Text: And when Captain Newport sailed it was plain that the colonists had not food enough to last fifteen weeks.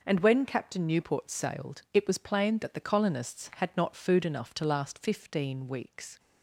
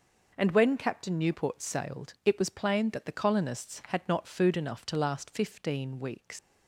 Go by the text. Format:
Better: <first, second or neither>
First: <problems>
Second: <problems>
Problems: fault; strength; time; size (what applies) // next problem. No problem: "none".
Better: first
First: none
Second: leaves "weeks" unfinished; at 6.3 s; 115 ms